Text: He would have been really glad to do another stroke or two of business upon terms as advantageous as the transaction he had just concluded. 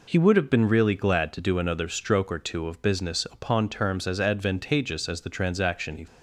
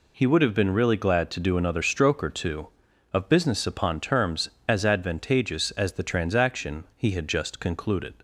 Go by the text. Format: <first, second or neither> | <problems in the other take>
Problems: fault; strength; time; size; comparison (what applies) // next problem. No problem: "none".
second | stops before "had just concluded"; at 6.0 s